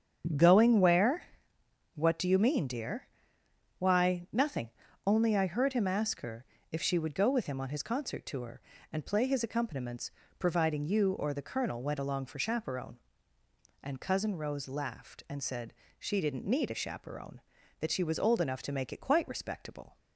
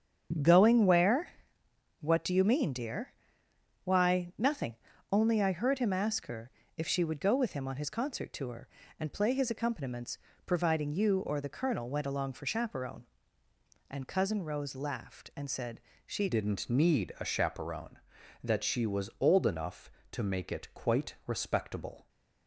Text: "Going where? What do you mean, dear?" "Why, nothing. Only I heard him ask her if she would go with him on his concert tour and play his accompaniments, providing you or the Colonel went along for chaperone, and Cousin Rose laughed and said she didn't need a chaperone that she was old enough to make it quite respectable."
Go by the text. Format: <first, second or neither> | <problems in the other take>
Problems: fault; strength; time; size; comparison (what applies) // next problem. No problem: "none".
first | starts louder than the rest; strong; until 2.1 s; 8 dB; strong in the first // pauses between "her" and "if"; slight; at 6.4 s; 0.28 s long; slight in the first // pauses between "said" and "she"; slight; at 15.8 s; 0.24 s long; slight in the first // changes voice at "didn't"; from 16.2 s on; 5.8 s long